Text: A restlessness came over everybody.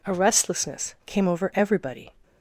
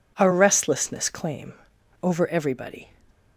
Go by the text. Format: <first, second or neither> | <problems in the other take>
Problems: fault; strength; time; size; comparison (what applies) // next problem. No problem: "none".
first | says "claim" for "came"; at 1.0 s